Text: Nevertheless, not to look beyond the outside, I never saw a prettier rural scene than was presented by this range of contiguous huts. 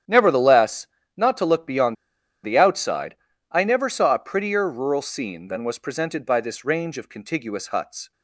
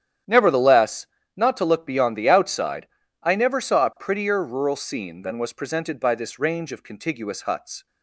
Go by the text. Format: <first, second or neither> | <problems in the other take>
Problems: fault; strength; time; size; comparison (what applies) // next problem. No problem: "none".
second | starts louder than the rest; strong; until 1.3 s; 10 dB; strong in the second // pauses between "beyond" and "the"; noticeable; at 1.9 s; 0.50 s long